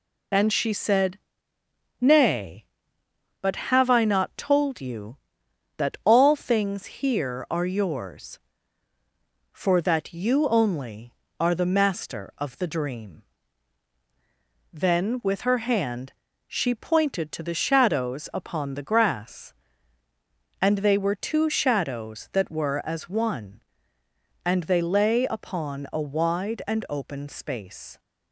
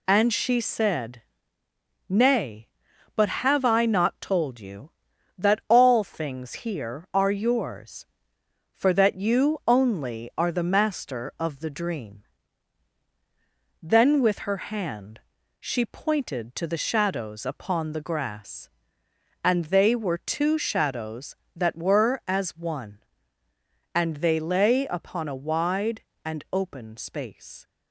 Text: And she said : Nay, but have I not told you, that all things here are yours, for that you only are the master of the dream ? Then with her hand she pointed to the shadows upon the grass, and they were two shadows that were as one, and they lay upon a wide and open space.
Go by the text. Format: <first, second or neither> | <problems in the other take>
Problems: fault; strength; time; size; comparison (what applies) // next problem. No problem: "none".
neither | pauses between "hand" and "she"; the same in both